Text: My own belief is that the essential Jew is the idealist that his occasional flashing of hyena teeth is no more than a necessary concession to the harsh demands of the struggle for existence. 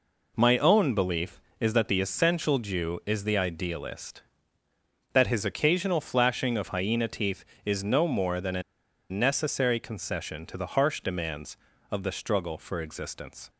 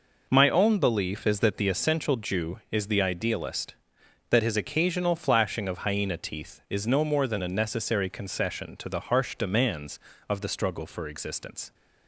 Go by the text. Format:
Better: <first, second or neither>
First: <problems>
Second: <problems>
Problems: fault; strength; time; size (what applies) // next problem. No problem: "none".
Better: second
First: pauses between "a" and "necessary"; noticeable; at 8.6 s; 0.47 s long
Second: none